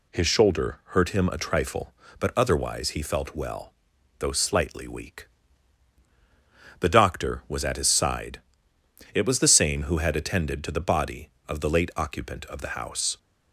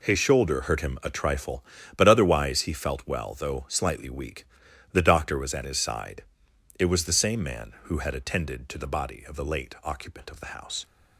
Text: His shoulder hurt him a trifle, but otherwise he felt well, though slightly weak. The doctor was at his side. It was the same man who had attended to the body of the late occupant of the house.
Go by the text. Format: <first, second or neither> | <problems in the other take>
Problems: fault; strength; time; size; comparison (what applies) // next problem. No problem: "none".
second | skips "man"; at 9.8 s